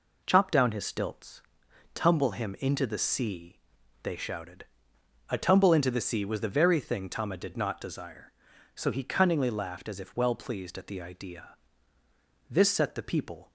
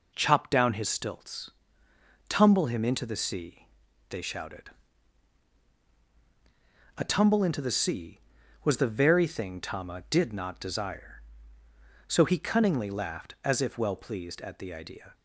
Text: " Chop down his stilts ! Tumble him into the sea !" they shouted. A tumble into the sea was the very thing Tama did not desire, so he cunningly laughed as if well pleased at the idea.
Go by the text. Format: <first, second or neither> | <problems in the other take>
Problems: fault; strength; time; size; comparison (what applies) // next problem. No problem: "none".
second | goes on to say "This set the people"; noticeable; from 12.4 s on; 1.0 s long